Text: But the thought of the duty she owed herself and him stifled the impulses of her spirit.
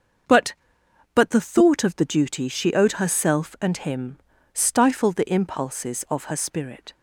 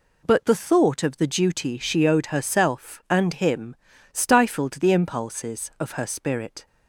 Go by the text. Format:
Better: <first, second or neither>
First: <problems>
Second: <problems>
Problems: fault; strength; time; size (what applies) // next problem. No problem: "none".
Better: second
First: starts louder than the rest; until 1.8 s; 6.5 dB // says "But" twice; at 1.1 s // pauses between "him" and "stifled"; slight; at 4.1 s; 0.36 s long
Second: pauses between "him" and "stifled"; slight; at 3.7 s; 0.36 s long